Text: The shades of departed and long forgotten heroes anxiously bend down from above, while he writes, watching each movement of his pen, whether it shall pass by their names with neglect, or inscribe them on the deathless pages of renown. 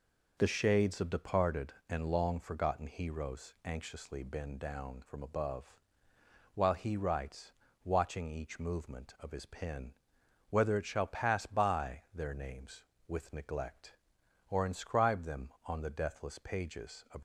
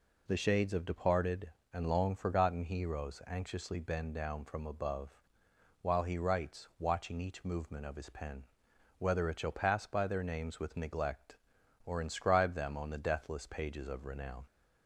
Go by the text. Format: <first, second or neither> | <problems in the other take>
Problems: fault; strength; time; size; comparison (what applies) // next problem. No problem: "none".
second | stops before "renown"; at 17.1 s